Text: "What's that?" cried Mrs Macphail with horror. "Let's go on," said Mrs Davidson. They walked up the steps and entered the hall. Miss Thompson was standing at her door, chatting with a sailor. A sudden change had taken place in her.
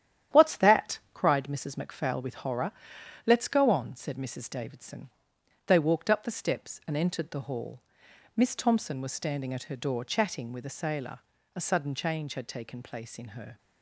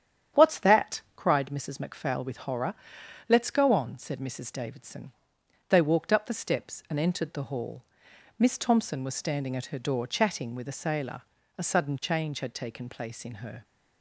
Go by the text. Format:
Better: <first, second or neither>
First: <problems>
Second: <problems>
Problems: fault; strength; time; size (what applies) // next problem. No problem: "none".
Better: second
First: gets quieter; noticeable; throughout; 5.5 dB // starts louder than the rest; strong; until 1.4 s; 10.5 dB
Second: starts louder than the rest; strong; until 1.4 s; 9.5 dB